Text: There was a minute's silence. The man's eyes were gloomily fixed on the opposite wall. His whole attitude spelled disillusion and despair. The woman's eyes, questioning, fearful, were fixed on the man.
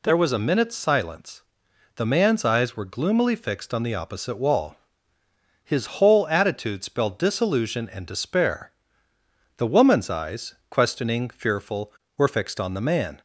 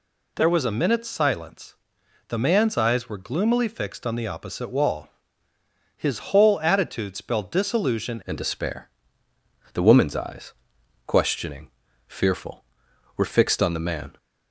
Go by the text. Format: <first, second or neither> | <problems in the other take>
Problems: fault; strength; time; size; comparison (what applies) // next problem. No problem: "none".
first | changes voice at "and"; from 8.2 s on; 5.9 s long